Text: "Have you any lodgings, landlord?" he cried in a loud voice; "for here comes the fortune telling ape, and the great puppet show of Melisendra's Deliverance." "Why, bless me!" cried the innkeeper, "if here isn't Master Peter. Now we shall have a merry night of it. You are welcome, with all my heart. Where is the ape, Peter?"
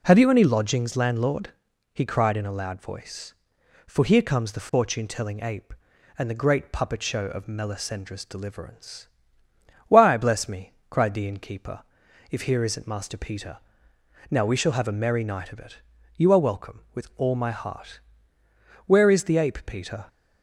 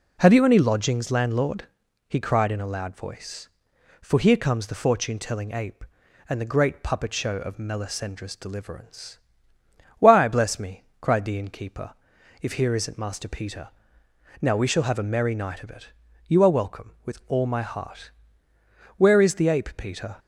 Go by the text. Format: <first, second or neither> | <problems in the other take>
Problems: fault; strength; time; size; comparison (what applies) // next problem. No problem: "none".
neither | none